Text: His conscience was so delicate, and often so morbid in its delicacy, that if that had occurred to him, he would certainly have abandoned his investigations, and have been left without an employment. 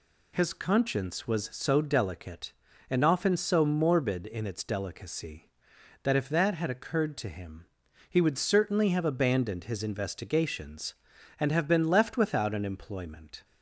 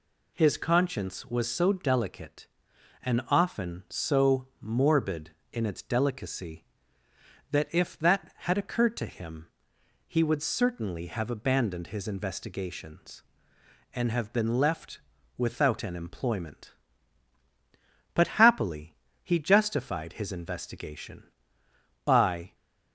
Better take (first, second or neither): first